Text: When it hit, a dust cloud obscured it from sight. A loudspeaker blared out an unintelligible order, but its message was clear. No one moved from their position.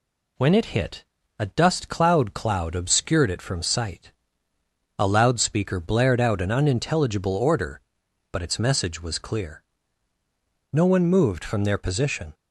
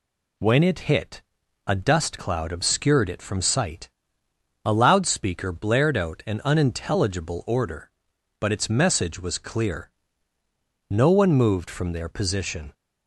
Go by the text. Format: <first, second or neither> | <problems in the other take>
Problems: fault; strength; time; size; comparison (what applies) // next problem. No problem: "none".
second | says "cloud" twice; at 2.3 s